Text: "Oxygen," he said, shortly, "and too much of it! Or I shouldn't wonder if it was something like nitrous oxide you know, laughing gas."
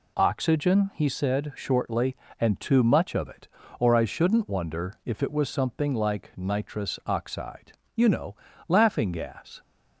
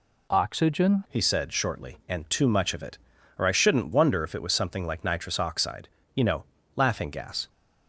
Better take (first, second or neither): first